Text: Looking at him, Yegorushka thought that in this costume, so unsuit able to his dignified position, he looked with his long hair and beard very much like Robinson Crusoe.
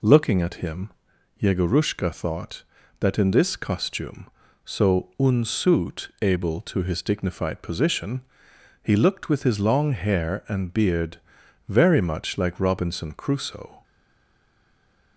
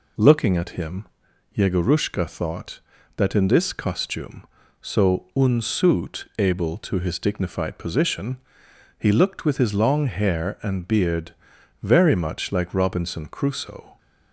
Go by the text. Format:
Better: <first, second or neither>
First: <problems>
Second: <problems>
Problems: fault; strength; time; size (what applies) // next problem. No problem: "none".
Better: second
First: pauses between "beard" and "very"; noticeable; at 11.2 s; 0.48 s long // stays silent after the last word; noticeable; from 13.8 s on; 1.3 s long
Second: pauses between "beard" and "very"; noticeable; at 11.3 s; 0.48 s long